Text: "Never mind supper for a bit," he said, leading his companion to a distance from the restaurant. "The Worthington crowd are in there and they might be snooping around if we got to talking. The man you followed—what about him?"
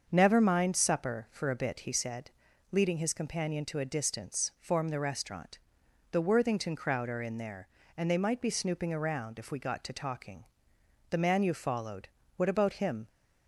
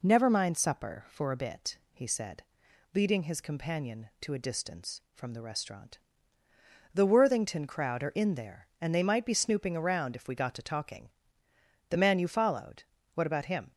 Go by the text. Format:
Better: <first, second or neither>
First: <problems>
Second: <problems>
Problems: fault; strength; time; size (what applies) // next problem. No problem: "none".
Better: second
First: starts louder than the rest; until 1.1 s; 6.5 dB // says "form" for "from"; at 4.5 s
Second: none